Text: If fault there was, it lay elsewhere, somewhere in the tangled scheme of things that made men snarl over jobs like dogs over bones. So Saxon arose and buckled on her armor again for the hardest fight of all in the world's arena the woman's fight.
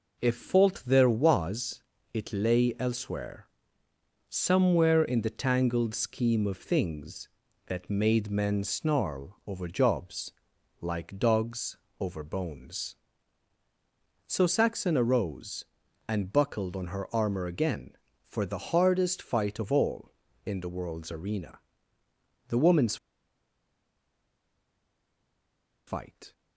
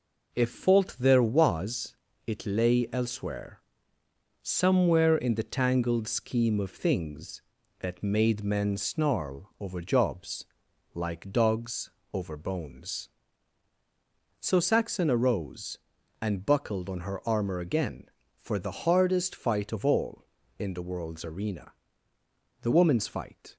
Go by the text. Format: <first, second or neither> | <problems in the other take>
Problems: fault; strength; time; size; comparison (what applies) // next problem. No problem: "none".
second | pauses between "jobs" and "like"; noticeable; at 10.3 s; 0.50 s long; noticeable in the second // pauses between "dogs" and "over"; slight; at 11.7 s; 0.24 s long; slight in the second // pauses between "arena" and "the"; noticeable; at 21.5 s; 0.88 s long; noticeable in the second // pauses between "woman's" and "fight"; strong; at 22.9 s; 2.9 s long